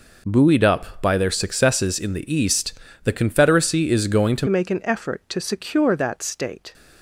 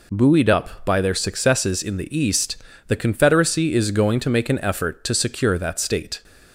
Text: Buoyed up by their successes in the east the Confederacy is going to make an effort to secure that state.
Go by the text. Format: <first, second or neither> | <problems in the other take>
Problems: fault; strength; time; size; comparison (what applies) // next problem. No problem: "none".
second | pauses between "east" and "the"; slight; at 2.7 s; 0.30 s long; slight in the second // changes voice at "make"; from 4.4 s on; 2.3 s long